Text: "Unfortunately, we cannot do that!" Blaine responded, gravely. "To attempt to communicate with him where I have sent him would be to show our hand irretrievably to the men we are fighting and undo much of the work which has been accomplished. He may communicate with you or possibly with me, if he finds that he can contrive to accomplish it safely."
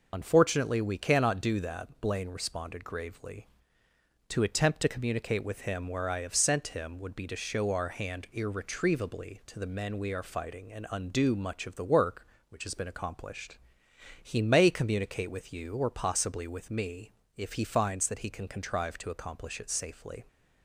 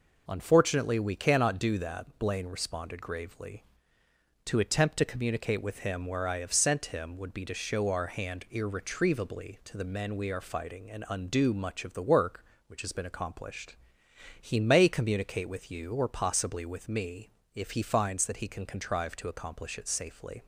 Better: second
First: loses the start of "Unfortunately"; at 0.1 s; 35 ms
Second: none

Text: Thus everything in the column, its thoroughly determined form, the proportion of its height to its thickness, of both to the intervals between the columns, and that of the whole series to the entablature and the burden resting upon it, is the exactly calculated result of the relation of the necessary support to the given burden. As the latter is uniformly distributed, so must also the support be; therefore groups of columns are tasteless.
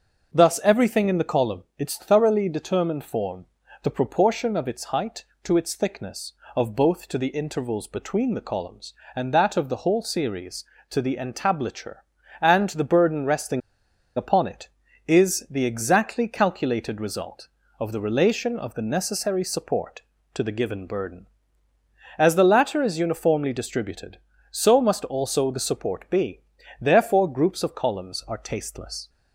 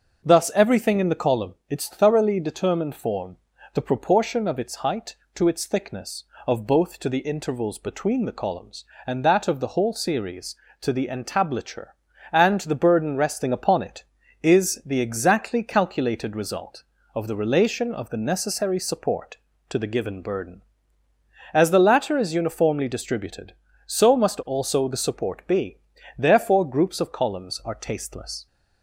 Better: second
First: starts louder than the rest; until 1.3 s; 6 dB // pauses between "resting" and "upon"; noticeable; at 13.6 s; 0.56 s long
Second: starts louder than the rest; until 1.2 s; 6 dB

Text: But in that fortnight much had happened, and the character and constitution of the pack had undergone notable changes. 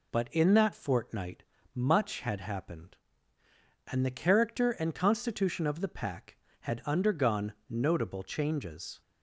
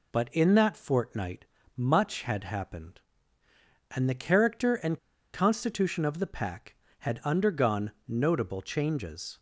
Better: first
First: pauses between "fortnight" and "much"; slight; at 1.4 s; 0.32 s long // pauses between "undergone" and "notable"; slight; at 7.5 s; 0.16 s long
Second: pauses between "fortnight" and "much"; slight; at 1.4 s; 0.32 s long // pauses between "and" and "constitution"; slight; at 4.9 s; 0.35 s long // pauses between "undergone" and "notable"; slight; at 7.9 s; 0.16 s long

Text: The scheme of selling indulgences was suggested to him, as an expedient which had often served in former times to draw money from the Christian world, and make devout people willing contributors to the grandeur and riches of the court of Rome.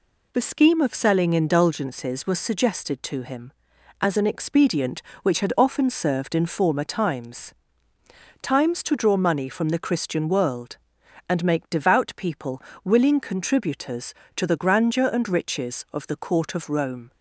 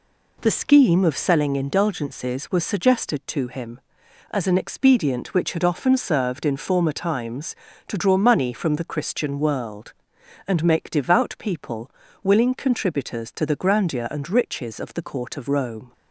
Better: second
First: says "times" twice; at 8.4 s // pauses between "people" and "willing"; slight; at 12.6 s; 0.22 s long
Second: pauses between "people" and "willing"; slight; at 11.8 s; 0.32 s long

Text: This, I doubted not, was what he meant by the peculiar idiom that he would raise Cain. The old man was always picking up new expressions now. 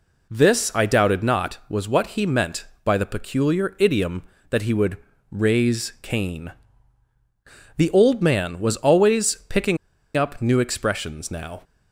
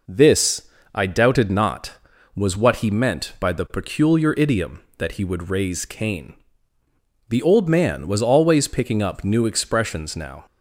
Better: second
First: pauses between "would" and "raise"; slight; at 4.9 s; 0.32 s long // pauses between "picking" and "up"; at 9.7 s; 0.40 s long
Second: none

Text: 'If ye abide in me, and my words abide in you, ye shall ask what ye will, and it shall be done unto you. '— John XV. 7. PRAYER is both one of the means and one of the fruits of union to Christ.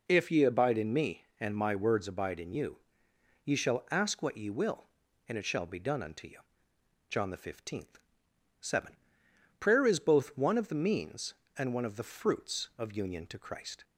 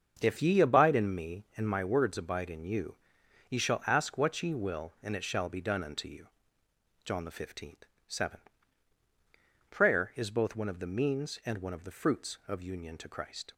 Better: first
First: none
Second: starts louder than the rest; until 1.5 s; 7 dB

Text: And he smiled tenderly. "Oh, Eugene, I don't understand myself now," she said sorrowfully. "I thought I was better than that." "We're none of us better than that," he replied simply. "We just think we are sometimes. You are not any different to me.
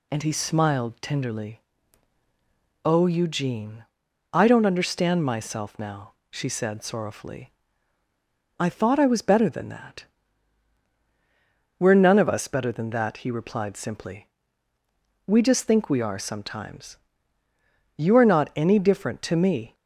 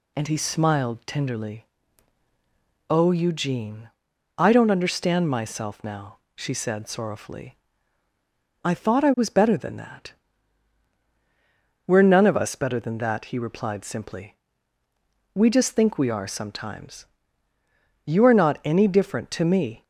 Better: neither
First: none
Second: none

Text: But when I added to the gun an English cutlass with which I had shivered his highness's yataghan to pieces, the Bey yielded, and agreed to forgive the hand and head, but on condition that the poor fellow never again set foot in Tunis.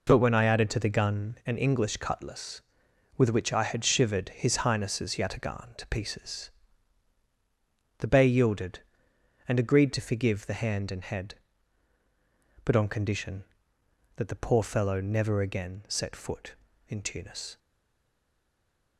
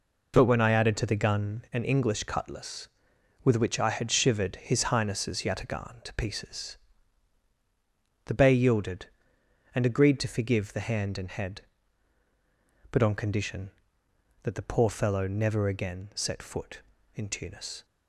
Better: second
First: stays silent after the last word; noticeable; from 17.5 s on; 1.4 s long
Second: none

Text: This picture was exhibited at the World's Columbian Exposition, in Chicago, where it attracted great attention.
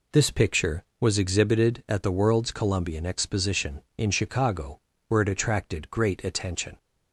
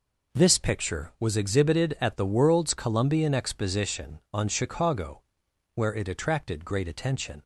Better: first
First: none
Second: says "on" for "in"; at 4.3 s

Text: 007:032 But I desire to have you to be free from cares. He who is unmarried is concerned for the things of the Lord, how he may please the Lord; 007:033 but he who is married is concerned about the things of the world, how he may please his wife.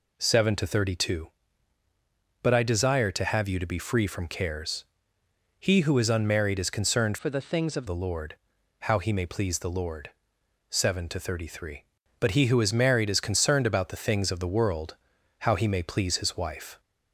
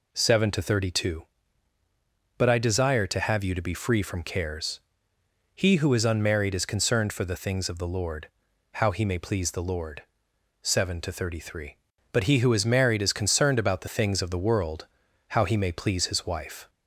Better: second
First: changes voice from "for" to "of"; from 7.1 to 7.8 s; 0.7 s long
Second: none

